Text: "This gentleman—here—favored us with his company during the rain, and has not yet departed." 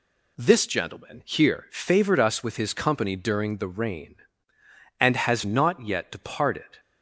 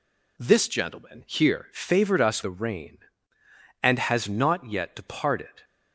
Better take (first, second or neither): first